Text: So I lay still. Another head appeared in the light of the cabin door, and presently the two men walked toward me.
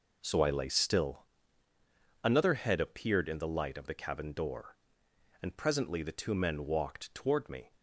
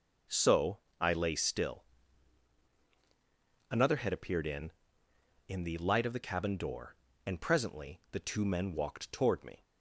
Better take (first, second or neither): first